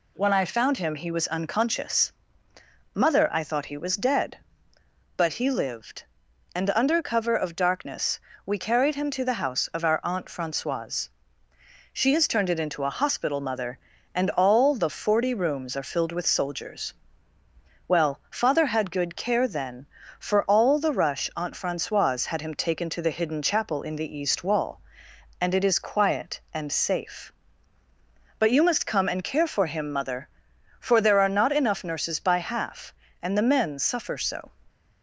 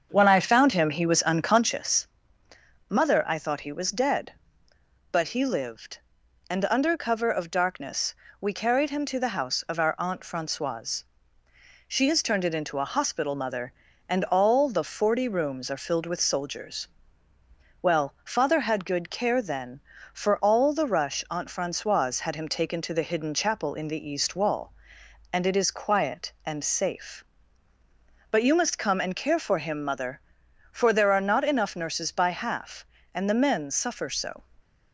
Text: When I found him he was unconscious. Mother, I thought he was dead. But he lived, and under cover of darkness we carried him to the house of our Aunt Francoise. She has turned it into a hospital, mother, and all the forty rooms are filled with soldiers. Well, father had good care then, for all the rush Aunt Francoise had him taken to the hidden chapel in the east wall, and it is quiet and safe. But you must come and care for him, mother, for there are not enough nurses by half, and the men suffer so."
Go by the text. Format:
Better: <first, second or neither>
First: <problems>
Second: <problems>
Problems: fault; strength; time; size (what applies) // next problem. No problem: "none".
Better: first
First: pauses between "darkness" and "we"; slight; at 8.2 s; 0.26 s long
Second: starts louder than the rest; until 1.8 s; 7 dB // pauses between "darkness" and "we"; slight; at 8.1 s; 0.26 s long